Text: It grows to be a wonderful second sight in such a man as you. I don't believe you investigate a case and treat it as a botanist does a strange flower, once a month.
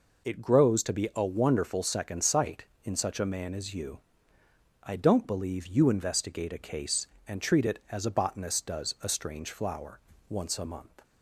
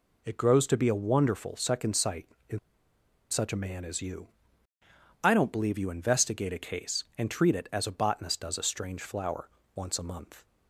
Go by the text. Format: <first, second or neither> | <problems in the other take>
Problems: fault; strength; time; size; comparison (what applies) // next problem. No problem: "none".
first | pauses between "in" and "such"; noticeable; at 2.5 s; 0.71 s long